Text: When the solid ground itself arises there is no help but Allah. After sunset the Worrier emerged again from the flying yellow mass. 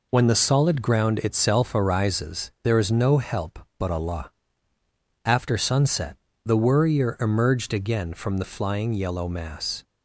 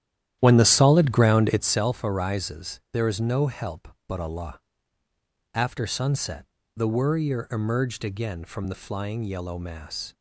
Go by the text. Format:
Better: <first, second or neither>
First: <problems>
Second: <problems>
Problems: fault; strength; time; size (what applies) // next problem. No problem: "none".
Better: first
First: pauses between "sunset" and "the"; slight; at 6.1 s; 0.28 s long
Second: starts louder than the rest; strong; until 1.8 s; 11.5 dB // pauses between "sunset" and "the"; slight; at 6.4 s; 0.30 s long